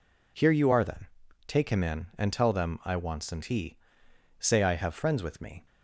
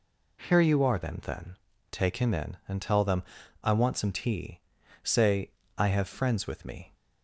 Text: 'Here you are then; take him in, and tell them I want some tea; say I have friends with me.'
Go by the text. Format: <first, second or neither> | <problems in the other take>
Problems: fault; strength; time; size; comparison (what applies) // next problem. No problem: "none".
first | says "then" twice; at 1.2 s // pauses between "them" and "I"; at 3.2 s; 0.38 s long // pauses between "say" and "I"; slight; at 5.4 s; 0.26 s long